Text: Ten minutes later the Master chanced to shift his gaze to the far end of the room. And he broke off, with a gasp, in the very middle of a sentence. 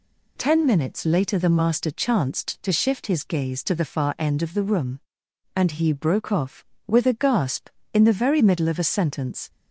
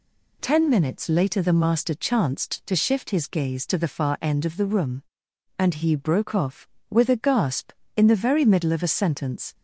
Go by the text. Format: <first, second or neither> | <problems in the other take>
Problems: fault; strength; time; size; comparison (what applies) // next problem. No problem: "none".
neither | none